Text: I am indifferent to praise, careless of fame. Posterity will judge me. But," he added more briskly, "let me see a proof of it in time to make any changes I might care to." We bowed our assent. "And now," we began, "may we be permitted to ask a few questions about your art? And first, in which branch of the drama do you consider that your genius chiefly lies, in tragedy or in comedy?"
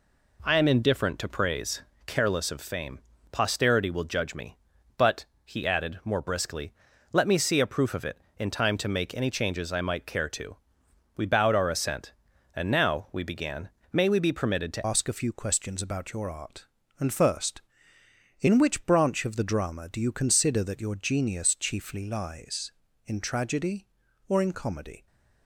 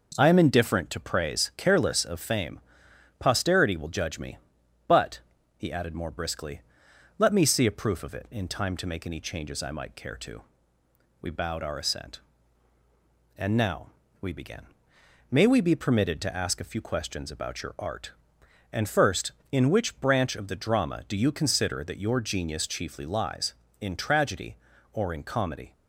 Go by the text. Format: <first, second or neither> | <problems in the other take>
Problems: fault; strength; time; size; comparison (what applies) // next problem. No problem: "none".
second | changes voice at "ask"; from 14.8 s on; 10.2 s long